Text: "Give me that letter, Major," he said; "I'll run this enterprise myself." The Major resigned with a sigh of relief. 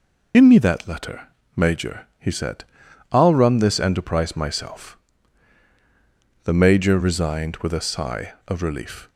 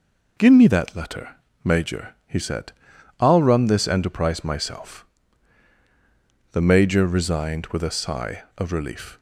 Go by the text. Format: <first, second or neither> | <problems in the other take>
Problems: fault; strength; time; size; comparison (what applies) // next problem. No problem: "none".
second | loses the start of "Give"; at 0.3 s; 60 ms